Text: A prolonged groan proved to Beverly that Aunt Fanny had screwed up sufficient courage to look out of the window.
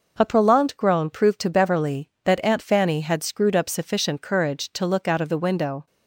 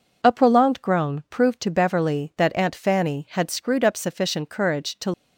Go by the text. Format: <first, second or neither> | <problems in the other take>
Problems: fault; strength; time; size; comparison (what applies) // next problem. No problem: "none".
first | stops before "look out of the window"; at 5.1 s